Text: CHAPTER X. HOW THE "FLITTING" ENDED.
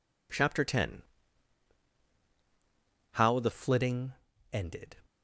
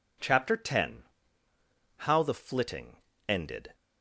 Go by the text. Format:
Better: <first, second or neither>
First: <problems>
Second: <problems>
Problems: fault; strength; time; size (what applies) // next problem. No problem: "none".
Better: second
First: changes voice at "FLITTING"; from 3.5 s on; 1.4 s long // pauses between "FLITTING" and "ENDED"; at 4.1 s; 0.40 s long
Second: pauses between "FLITTING" and "ENDED"; slight; at 2.9 s; 0.32 s long